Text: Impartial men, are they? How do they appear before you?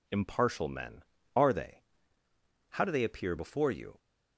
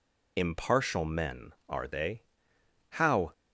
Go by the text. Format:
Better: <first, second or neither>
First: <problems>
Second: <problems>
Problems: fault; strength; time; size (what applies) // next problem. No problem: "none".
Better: first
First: none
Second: stops before "do they appear before you"; at 3.3 s